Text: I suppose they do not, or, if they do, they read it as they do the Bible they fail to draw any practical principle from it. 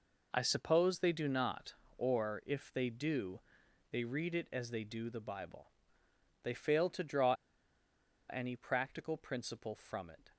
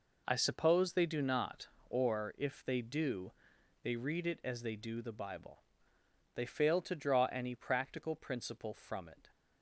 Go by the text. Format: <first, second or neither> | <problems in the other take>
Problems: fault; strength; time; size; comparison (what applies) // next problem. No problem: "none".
second | pauses between "Bible" and "they"; noticeable; at 5.6 s; 0.76 s long; noticeable in the second // pauses between "draw" and "any"; noticeable; at 7.3 s; 0.95 s long